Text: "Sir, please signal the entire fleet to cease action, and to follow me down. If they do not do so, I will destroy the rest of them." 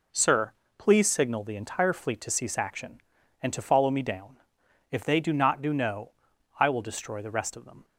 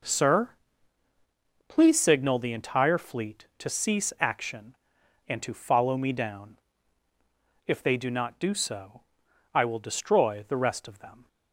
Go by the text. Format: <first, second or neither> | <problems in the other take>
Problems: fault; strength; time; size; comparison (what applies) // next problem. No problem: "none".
second | says "no" for "so"; at 5.7 s